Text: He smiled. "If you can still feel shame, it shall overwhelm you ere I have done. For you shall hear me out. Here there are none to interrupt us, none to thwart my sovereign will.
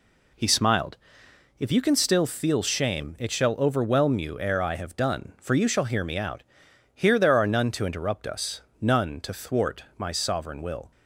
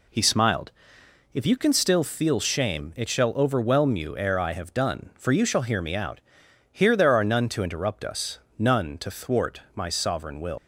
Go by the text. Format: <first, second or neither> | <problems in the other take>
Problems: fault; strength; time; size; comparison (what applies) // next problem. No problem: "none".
first | leaves "will" unfinished; at 10.5 s; 115 ms